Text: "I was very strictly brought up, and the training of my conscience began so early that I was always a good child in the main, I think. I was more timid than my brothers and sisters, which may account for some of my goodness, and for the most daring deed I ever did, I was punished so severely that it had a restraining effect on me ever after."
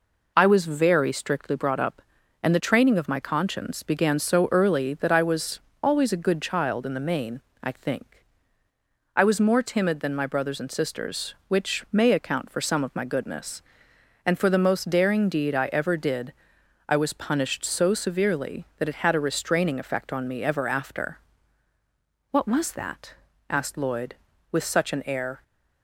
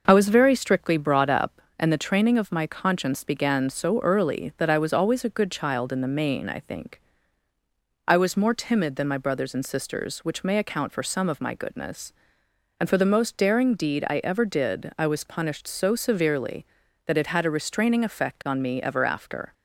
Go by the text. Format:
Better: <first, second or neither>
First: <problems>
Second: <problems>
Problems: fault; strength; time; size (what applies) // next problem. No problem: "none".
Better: second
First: pauses between "was" and "always"; slight; at 5.6 s; 0.22 s long // goes on to say "What was that asked Lloyd with such an air"; strong; from 22.3 s on; 3.1 s long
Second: none